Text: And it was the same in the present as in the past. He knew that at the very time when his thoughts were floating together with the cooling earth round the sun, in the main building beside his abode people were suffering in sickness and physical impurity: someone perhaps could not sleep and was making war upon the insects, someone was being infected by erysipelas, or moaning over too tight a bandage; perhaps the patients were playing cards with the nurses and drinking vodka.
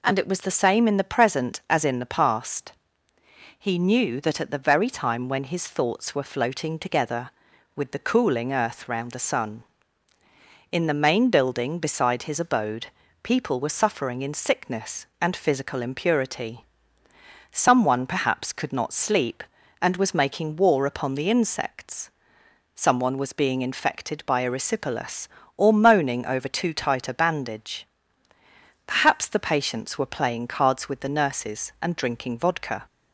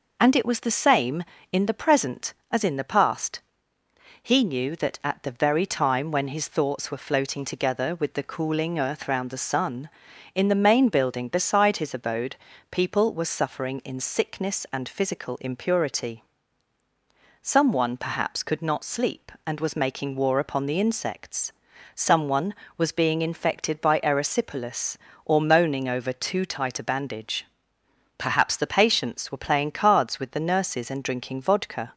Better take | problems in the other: neither | pauses between "abode" and "people"; slight; the same in both

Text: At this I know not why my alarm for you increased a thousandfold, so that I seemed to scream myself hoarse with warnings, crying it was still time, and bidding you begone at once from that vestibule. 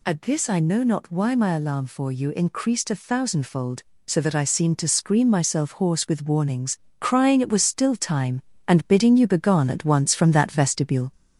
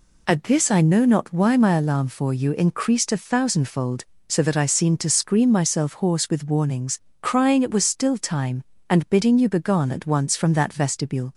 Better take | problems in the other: second | gets louder; slight; throughout; 2.5 dB

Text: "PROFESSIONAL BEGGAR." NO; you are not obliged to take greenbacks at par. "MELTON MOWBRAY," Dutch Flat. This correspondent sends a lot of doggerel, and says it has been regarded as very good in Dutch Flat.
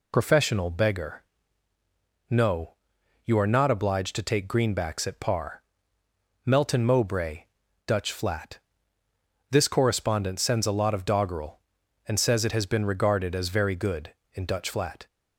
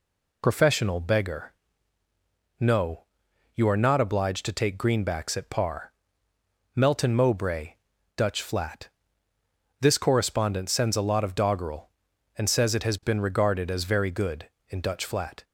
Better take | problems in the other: neither | none

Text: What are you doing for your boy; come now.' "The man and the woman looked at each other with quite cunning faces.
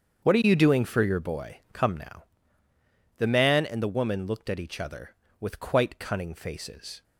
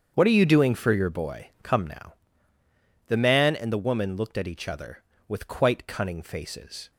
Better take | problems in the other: neither | starts louder than the rest; strong; the same in both

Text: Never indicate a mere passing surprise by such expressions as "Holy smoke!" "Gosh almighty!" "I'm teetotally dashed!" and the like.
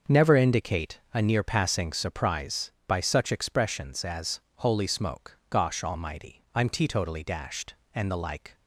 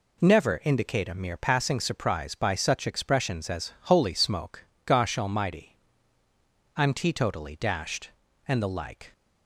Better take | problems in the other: second | starts louder than the rest; noticeable; until 1.2 s; 6 dB // pauses between "indicate" and "a"; slight; at 0.9 s; 0.16 s long // says "near" for "mere"; at 1.2 s // pauses between "as" and "Holy"; slight; at 4.3 s; 0.18 s long

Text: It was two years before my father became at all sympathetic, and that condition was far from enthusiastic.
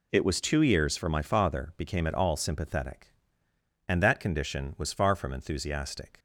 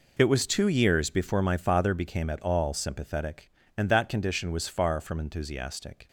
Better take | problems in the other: second | says "for" for "before"; at 0.9 s

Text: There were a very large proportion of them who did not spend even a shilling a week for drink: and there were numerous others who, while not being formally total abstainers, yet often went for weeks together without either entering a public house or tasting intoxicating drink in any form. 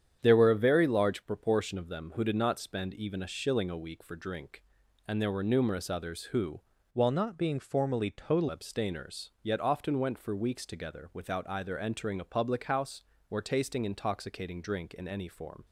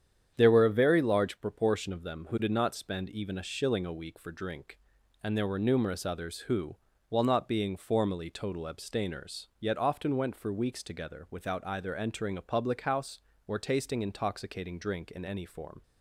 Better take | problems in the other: second | starts louder than the rest; strong; until 1.2 s; 9 dB; strong in the second // changes voice from "while" to "total"; from 6.9 to 8.4 s; 1.5 s long

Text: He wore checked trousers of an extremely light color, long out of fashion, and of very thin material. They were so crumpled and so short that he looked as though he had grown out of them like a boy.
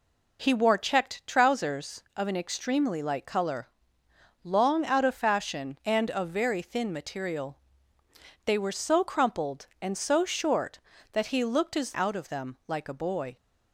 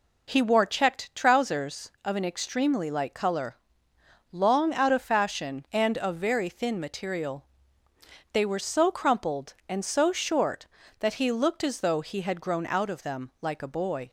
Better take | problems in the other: second | skips "though he had grown"; at 11.9 s

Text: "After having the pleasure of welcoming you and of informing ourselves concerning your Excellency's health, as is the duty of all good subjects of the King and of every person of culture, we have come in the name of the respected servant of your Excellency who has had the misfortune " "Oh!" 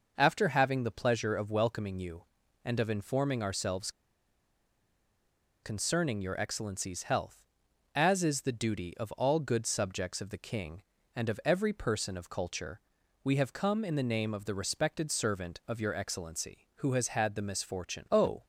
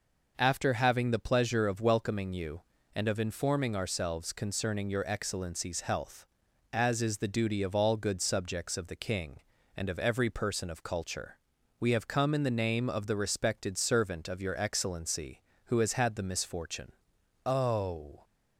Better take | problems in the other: second | pauses between "ourselves" and "concerning"; strong; at 3.8 s; 1.7 s long

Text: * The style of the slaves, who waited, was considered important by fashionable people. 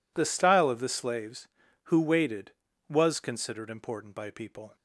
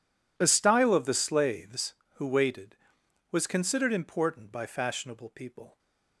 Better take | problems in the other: second | skips "fashionable"; at 4.2 s

